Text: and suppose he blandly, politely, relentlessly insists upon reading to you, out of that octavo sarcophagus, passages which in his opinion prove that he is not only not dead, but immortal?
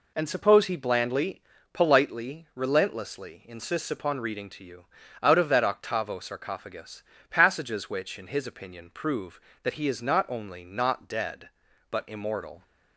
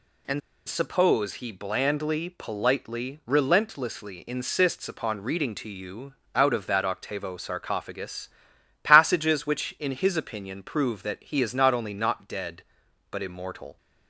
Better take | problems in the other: first | pauses between "and" and "suppose"; slight; at 0.4 s; 0.28 s long

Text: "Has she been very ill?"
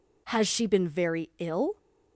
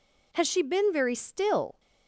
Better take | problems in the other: first | says "still" for "ill"; at 1.1 s

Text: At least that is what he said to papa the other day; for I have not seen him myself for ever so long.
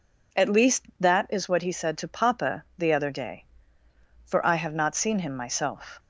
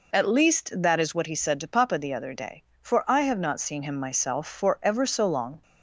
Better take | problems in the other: second | stops before "for ever so long"; at 5.9 s

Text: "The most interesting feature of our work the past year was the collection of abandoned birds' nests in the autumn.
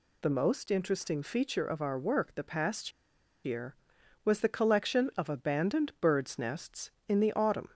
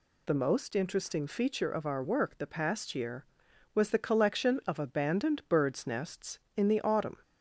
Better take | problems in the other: second | pauses between "past" and "year"; noticeable; at 2.9 s; 0.53 s long

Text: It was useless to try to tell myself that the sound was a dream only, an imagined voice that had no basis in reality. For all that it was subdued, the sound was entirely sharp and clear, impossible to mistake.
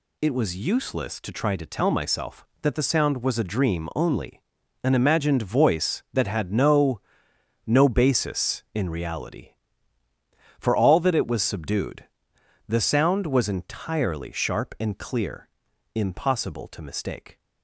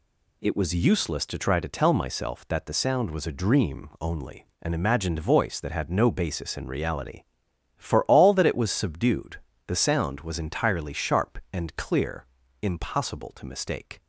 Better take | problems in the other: second | says "no" twice; at 7.6 s

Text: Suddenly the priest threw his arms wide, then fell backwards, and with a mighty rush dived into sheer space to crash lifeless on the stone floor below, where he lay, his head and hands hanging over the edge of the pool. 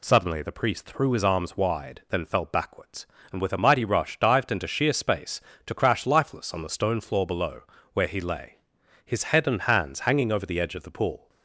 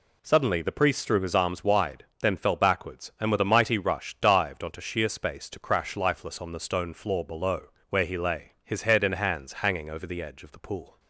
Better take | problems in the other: first | says "onto" for "into"; at 4.6 s

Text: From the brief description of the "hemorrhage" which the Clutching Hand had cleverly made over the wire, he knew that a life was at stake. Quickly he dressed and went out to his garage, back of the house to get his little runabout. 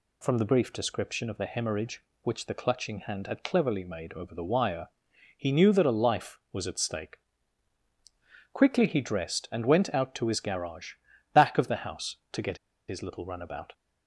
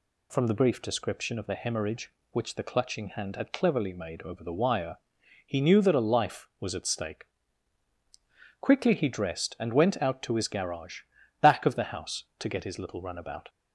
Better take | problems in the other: second | pauses between "get" and "his"; slight; at 12.5 s; 0.32 s long

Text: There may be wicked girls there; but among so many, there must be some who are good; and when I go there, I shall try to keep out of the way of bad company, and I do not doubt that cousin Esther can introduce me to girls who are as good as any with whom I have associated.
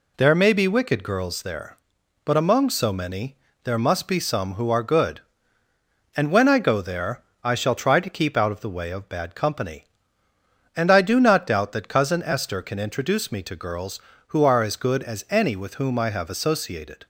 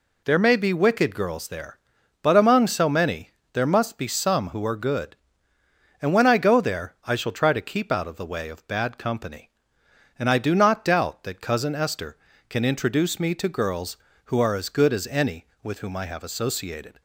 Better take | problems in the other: neither | none

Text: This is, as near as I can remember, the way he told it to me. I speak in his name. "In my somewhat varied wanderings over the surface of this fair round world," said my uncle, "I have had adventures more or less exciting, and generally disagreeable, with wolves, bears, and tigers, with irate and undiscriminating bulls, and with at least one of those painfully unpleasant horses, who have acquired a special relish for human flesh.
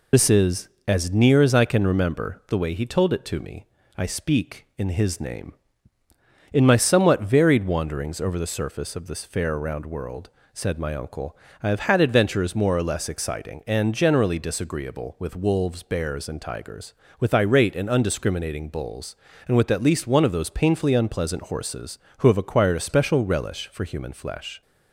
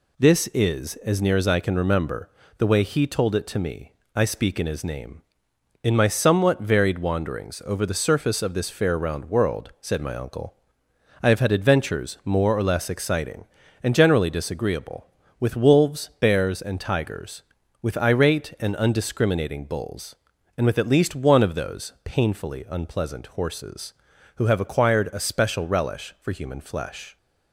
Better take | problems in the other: second | loses the start of "This"; at 0.1 s; 60 ms

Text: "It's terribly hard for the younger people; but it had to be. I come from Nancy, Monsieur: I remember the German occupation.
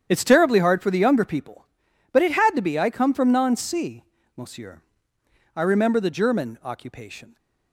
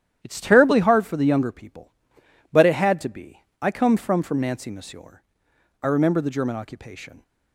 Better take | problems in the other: first | starts louder than the rest; strong; until 1.2 s; 10.5 dB; strong in the first // says "from" twice; at 4.2 s

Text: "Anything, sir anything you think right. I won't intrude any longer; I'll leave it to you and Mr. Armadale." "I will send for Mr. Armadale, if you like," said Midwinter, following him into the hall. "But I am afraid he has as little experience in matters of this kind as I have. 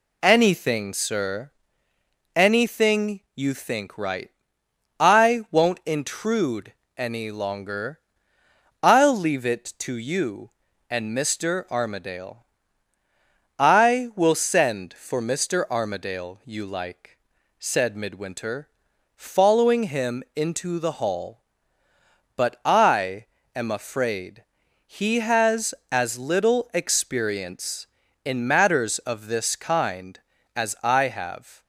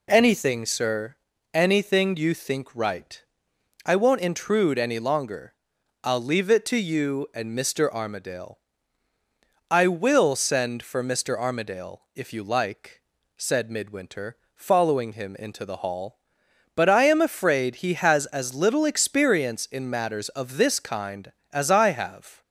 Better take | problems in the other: second | pauses between "sir" and "anything"; noticeable; at 1.5 s; 0.84 s long; slight in the second // pauses between "anything" and "you"; slight; at 3.1 s; 0.16 s long // pauses between "intrude" and "any"; slight; at 6.7 s; 0.24 s long // skips "if"; at 16.4 s // pauses between "I" and "am"; slight; at 23.2 s; 0.30 s long // pauses between "afraid" and "he"; at 24.4 s; 0.42 s long

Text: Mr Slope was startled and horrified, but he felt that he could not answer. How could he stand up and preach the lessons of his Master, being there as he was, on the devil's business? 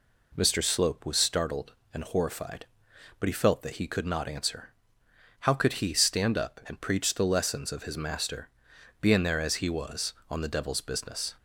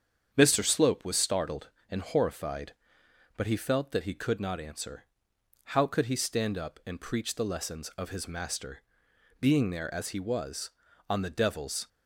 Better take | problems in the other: first | starts louder than the rest; strong; until 1.3 s; 7.5 dB // stops before "business"; at 11.8 s

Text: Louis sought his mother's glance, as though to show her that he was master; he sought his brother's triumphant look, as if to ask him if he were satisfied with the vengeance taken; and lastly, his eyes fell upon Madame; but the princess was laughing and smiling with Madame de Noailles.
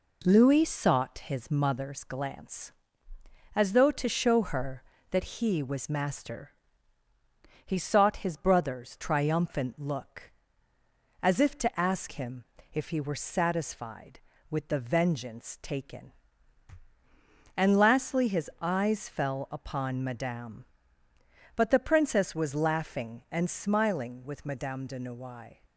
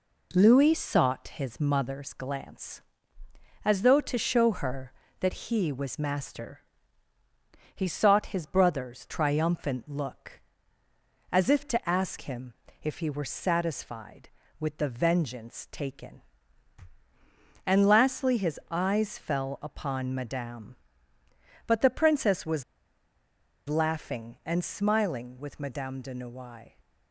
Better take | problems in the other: first | pauses between "him" and "if"; slight; at 12.5 s; 0.28 s long; slight in the first // pauses between "was" and "laughing"; at 22.6 s; 1.0 s long

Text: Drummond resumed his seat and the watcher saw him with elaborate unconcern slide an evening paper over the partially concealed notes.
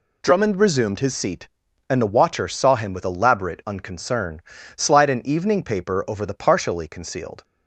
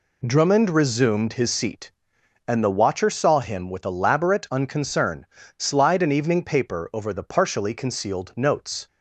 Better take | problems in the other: second | pauses between "unconcern" and "slide"; slight; at 4.4 s; 0.34 s long; slight in the second // stops before "notes"; at 7.4 s

